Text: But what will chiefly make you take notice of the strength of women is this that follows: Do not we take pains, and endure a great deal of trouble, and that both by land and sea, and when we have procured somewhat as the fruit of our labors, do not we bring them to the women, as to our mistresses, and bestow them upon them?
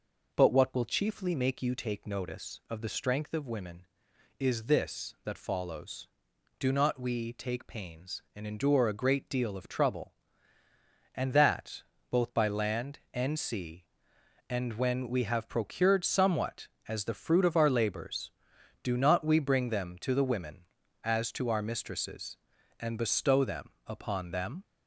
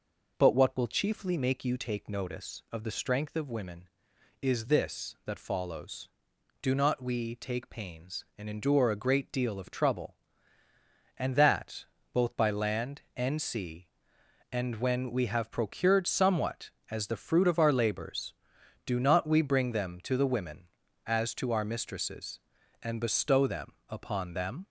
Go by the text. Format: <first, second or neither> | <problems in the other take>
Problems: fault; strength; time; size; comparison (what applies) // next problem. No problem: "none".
neither | pauses between "that" and "both"; slight; the same in both